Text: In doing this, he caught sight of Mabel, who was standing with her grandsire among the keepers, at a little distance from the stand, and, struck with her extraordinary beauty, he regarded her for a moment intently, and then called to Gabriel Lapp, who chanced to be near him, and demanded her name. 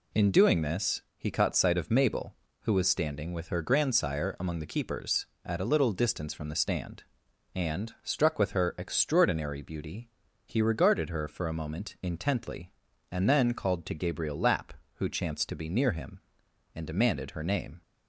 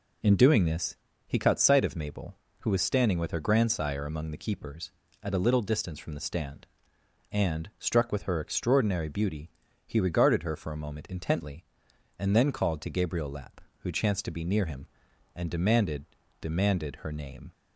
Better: first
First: none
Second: says "demanded" twice; at 16.4 s

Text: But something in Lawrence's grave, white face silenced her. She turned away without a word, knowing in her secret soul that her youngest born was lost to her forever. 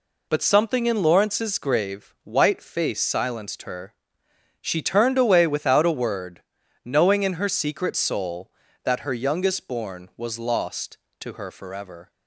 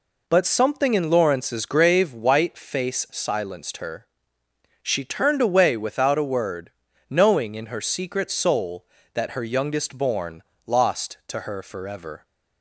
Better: first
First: none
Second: skips "was"; at 10.5 s

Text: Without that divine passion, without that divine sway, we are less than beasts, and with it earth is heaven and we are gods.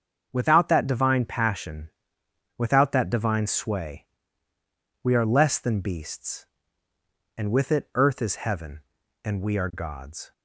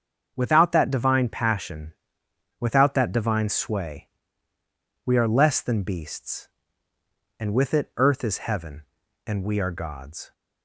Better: neither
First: starts louder than the rest; until 1.3 s; 7 dB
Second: starts louder than the rest; until 1.3 s; 7 dB

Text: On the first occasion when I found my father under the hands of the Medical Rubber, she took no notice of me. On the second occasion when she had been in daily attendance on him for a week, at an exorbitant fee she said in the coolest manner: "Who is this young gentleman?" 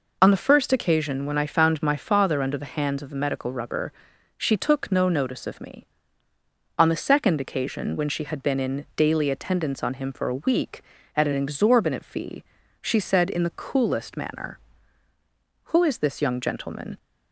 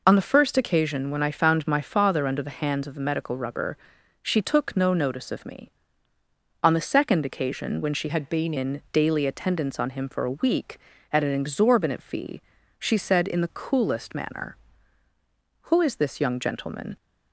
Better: first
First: pauses between "fee" and "she"; at 12.4 s; 0.40 s long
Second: changes voice from "had" to "been"; from 8.0 to 8.5 s; 0.5 s long // pauses between "fee" and "she"; at 12.4 s; 0.40 s long

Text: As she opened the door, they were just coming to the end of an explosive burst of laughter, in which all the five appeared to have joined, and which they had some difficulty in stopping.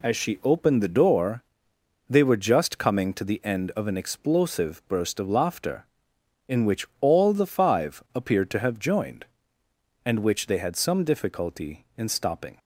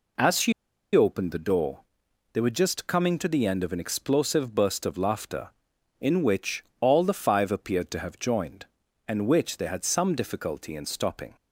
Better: first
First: none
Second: pauses between "she" and "opened"; at 0.5 s; 0.42 s long // pauses between "which" and "all"; slight; at 6.6 s; 0.16 s long

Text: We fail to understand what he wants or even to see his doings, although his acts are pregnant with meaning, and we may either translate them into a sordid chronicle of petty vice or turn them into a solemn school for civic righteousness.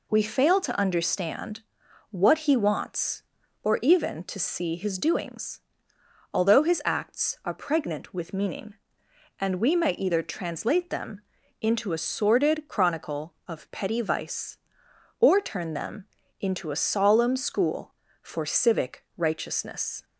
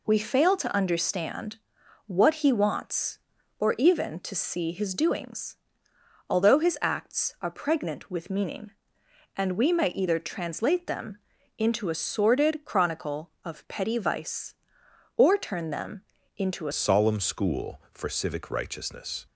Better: first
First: pauses between "understand" and "what"; noticeable; at 1.6 s; 0.48 s long // pauses between "them" and "into"; at 11.2 s; 0.40 s long // pauses between "them" and "into"; slight; at 16.0 s; 0.36 s long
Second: pauses between "understand" and "what"; noticeable; at 1.5 s; 0.48 s long // pauses between "them" and "into"; at 11.1 s; 0.40 s long // pauses between "them" and "into"; slight; at 16.0 s; 0.36 s long // changes voice at "solemn"; from 16.7 s on; 2.5 s long

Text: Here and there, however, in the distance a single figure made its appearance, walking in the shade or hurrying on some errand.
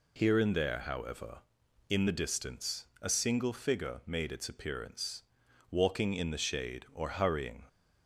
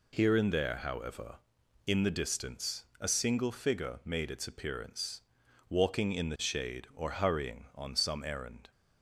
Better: second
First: pauses between "distance" and "a"; slight; at 2.8 s; 0.16 s long // stops before "on some errand"; at 7.6 s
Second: pauses between "distance" and "a"; slight; at 2.8 s; 0.16 s long

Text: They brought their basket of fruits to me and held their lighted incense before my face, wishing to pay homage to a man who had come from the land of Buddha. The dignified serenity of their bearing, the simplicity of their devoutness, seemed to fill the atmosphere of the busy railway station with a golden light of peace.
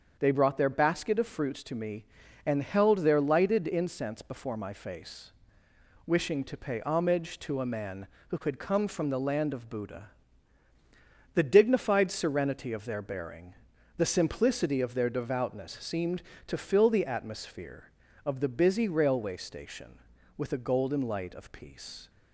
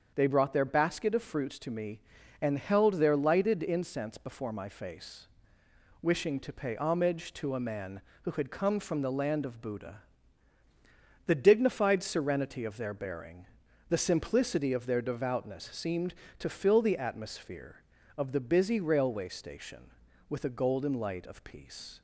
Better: neither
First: starts louder than the rest; until 1.2 s; 7 dB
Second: starts louder than the rest; until 1.1 s; 7 dB

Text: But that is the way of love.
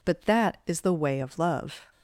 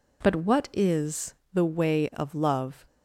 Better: first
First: none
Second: says "what" for "that"; at 0.3 s // pauses between "is" and "the"; slight; at 1.3 s; 0.18 s long

